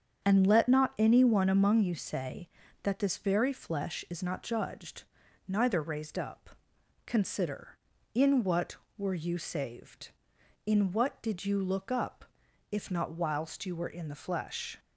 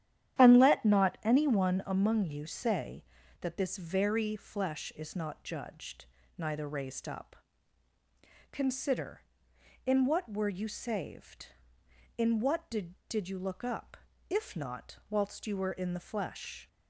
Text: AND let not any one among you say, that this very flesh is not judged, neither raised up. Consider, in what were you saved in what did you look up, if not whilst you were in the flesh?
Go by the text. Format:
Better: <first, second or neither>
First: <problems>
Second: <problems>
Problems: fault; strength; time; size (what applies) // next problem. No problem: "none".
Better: first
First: starts louder than the rest; strong; until 1.2 s; 7.5 dB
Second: starts louder than the rest; strong; until 1.4 s; 10.5 dB // says "did" twice; at 13.0 s